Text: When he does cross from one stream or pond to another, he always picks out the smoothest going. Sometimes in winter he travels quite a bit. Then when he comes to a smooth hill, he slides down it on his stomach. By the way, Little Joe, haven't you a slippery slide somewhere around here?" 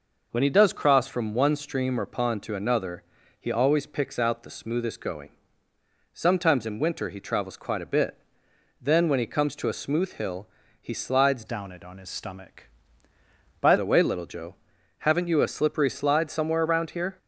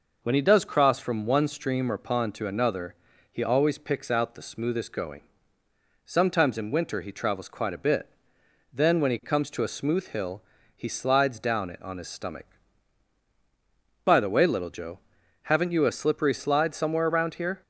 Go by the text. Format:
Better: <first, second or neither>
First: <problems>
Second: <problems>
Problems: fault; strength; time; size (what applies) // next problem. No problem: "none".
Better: second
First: changes voice from "down" to "By"; from 11.4 to 13.7 s; 2.3 s long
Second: none